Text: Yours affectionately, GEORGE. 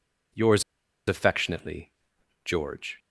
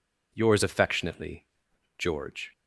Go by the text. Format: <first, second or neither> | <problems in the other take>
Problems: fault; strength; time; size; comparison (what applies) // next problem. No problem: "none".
second | pauses between "Yours" and "affectionately"; at 0.6 s; 0.45 s long